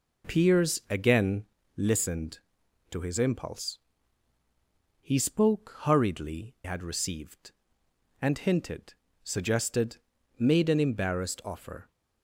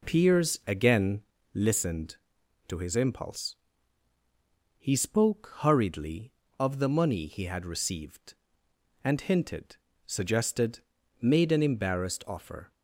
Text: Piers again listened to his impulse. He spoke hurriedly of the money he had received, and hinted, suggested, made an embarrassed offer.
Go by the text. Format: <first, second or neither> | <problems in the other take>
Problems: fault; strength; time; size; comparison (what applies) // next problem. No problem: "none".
second | pauses between "again" and "listened"; slight; at 1.4 s; 0.34 s long; slight in the second // skips "of the money he"; at 6.5 s